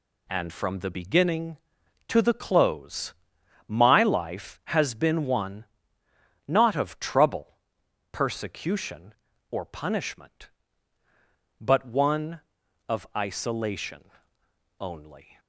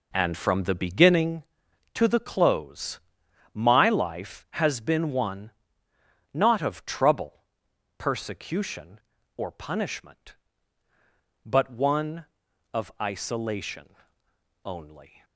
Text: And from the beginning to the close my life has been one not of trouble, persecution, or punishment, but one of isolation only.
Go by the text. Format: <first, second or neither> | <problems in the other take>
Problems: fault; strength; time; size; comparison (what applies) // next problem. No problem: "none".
first | starts louder than the rest; noticeable; until 1.4 s; 4 dB // pauses between "close" and "my"; noticeable; at 2.9 s; 0.54 s long; noticeable in the first // pauses between "one" and "not"; noticeable; at 5.5 s; 0.82 s long; noticeable in the first // pauses between "isolation" and "only"; noticeable; at 13.8 s; 0.76 s long; noticeable in the first